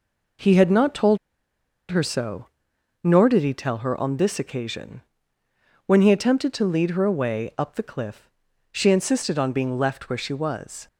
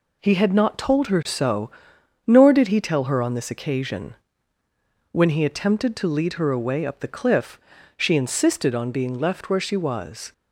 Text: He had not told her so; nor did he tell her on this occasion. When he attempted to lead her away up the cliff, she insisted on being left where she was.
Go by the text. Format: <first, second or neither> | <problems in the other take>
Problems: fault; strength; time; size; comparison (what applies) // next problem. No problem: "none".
second | pauses between "told" and "her"; noticeable; at 1.1 s; 0.73 s long